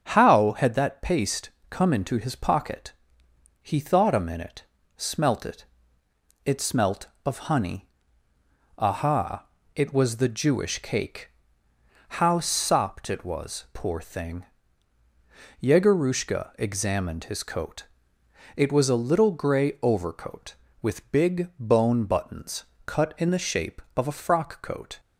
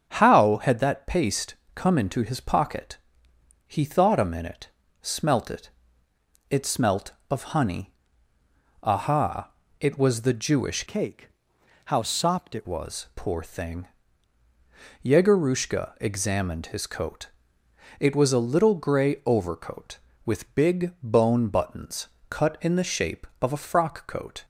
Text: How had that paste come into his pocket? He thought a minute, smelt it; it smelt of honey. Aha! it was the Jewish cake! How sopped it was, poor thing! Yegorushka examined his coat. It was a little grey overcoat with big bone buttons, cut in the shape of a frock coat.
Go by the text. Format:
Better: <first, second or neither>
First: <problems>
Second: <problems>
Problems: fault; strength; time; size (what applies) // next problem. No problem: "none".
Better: first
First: starts louder than the rest; until 1.0 s; 6.5 dB // pauses between "paste" and "come"; slight; at 1.5 s; 0.18 s long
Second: starts louder than the rest; until 1.1 s; 7 dB // pauses between "paste" and "come"; slight; at 1.5 s; 0.18 s long // changes voice from "cake" to "it"; from 10.8 to 12.6 s; 1.8 s long